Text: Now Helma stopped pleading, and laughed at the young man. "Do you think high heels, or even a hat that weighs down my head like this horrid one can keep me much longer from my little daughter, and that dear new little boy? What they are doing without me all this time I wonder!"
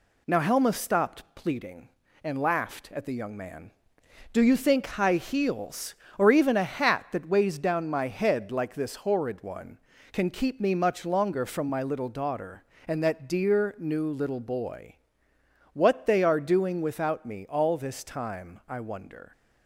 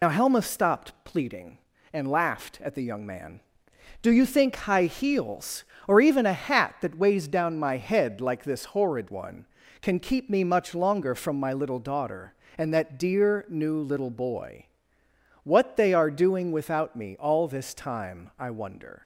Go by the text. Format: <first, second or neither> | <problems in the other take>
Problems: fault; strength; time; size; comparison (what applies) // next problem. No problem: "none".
first | loses the start of "Now"; at 0.0 s; 65 ms